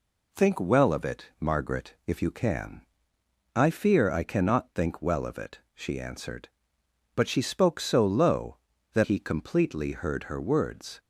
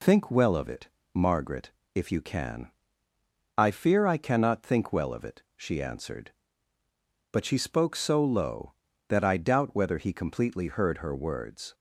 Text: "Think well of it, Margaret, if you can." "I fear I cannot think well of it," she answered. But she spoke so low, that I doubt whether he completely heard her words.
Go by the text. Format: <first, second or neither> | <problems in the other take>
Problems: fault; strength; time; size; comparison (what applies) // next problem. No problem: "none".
second | skips "I doubt whether"; at 9.0 s